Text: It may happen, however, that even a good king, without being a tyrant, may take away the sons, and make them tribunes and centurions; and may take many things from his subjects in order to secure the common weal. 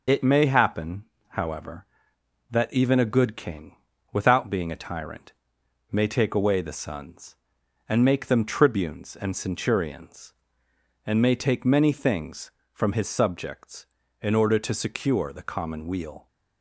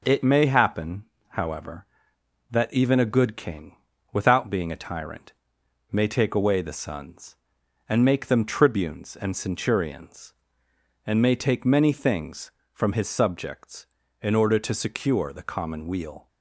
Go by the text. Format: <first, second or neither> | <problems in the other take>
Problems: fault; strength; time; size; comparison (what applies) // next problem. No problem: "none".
second | loses the start of "It"; at 0.0 s; 55 ms